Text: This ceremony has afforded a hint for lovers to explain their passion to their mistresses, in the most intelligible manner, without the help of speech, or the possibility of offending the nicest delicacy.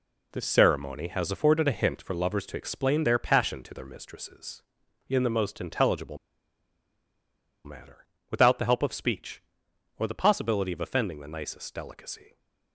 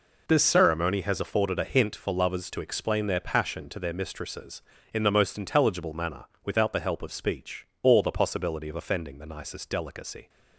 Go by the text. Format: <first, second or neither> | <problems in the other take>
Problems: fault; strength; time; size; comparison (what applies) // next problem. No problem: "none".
second | pauses between "intelligible" and "manner"; strong; at 6.1 s; 1.4 s long